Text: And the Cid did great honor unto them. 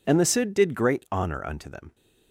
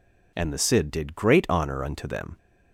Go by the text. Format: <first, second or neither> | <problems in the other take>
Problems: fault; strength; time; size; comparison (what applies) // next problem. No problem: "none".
neither | none